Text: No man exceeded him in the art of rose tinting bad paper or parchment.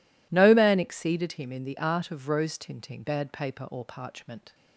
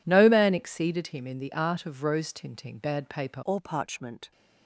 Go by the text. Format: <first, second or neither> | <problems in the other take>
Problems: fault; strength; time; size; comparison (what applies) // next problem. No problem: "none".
first | changes voice at "or"; from 3.4 s on; 0.9 s long